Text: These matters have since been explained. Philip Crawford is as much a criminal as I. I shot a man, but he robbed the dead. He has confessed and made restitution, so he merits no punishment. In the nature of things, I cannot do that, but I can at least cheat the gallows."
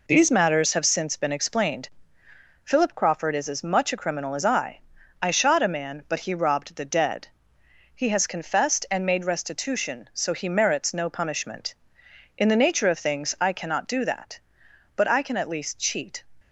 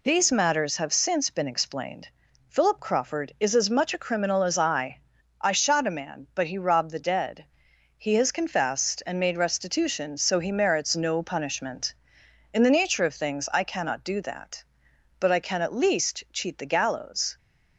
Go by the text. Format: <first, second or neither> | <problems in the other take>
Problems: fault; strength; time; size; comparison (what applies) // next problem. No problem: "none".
second | stops before "the gallows"; at 16.4 s